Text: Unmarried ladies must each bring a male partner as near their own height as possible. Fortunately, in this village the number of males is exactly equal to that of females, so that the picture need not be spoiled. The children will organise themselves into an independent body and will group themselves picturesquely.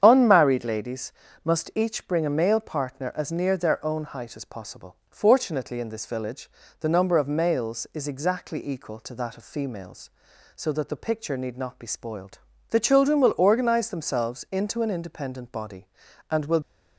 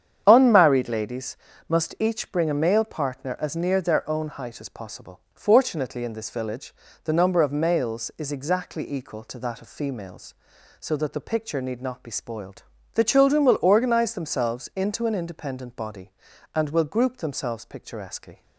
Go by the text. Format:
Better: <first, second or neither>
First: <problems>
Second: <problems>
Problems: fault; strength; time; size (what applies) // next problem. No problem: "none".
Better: second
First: starts louder than the rest; strong; until 1.0 s; 8 dB // pauses between "ladies" and "must"; slight; at 1.1 s; 0.32 s long // pauses between "village" and "the"; slight; at 6.4 s; 0.32 s long // stops before "group themselves picturesquely"; at 16.6 s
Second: starts louder than the rest; strong; until 1.2 s; 8 dB // pauses between "ladies" and "must"; slight; at 1.3 s; 0.32 s long // pauses between "village" and "the"; slight; at 6.7 s; 0.32 s long